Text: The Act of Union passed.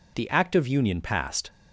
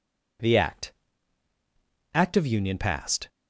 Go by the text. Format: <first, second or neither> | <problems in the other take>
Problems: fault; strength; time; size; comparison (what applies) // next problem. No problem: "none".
first | says "Act" twice; at 2.1 s